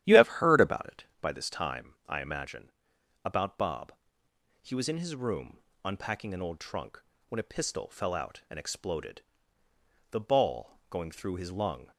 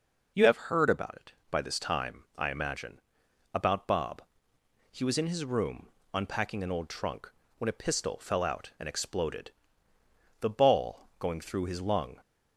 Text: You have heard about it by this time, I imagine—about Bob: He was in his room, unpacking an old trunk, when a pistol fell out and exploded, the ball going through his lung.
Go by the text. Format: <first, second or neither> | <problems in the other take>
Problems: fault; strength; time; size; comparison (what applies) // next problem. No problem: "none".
second | starts louder than the rest; strong; until 1.2 s; 11.5 dB